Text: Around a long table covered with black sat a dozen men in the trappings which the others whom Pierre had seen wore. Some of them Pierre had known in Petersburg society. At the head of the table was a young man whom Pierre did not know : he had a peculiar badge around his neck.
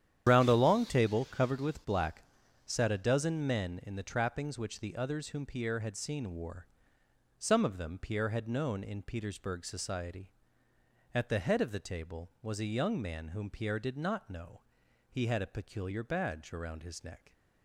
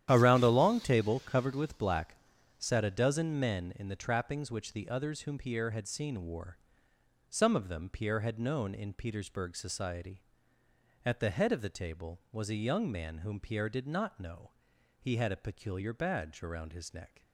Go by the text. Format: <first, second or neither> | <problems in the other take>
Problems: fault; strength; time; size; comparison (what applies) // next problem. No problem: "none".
second | loses the start of "Around"; at 0.2 s; 130 ms // starts louder than the rest; strong; until 1.2 s; 10.5 dB; strong in the second // pauses between "black" and "sat"; at 2.2 s; 0.42 s long; also in the second